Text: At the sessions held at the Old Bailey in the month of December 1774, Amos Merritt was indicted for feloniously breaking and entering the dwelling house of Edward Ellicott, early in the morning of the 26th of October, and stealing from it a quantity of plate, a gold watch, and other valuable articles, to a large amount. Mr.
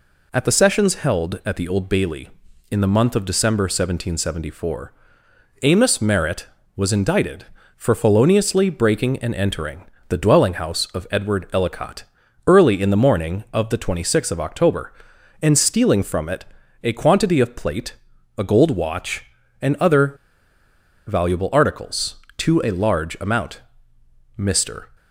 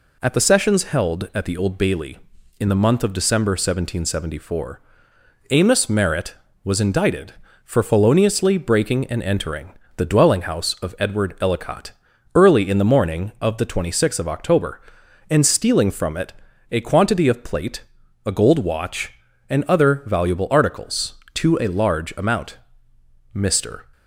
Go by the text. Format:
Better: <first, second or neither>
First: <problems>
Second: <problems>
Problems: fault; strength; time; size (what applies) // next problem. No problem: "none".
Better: second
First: pauses between "entering" and "the"; slight; at 9.8 s; 0.24 s long // pauses between "it" and "a"; at 16.4 s; 0.38 s long // pauses between "other" and "valuable"; noticeable; at 20.1 s; 0.93 s long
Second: pauses between "entering" and "the"; slight; at 9.7 s; 0.24 s long // pauses between "it" and "a"; at 16.3 s; 0.38 s long